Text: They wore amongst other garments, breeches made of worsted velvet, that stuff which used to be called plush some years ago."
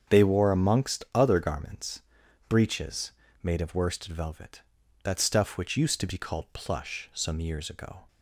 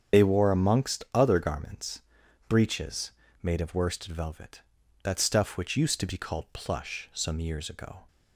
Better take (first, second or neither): first